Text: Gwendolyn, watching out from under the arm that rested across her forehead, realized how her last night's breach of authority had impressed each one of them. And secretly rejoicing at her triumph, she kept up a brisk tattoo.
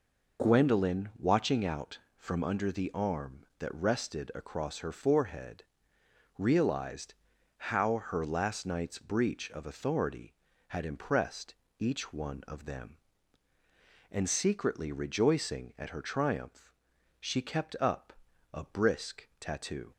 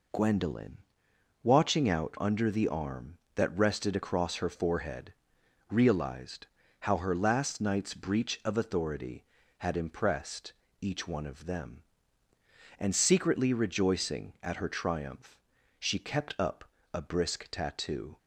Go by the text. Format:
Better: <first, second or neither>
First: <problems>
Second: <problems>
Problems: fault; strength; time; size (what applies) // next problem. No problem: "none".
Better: first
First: pauses between "realized" and "how"; at 7.1 s; 0.44 s long // pauses between "impressed" and "each"; slight; at 11.5 s; 0.26 s long // pauses between "up" and "a"; at 18.1 s; 0.40 s long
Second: skips "from"; at 2.1 s // pauses between "realized" and "how"; slight; at 6.4 s; 0.36 s long // pauses between "impressed" and "each"; slight; at 10.5 s; 0.28 s long // pauses between "up" and "a"; slight; at 16.6 s; 0.30 s long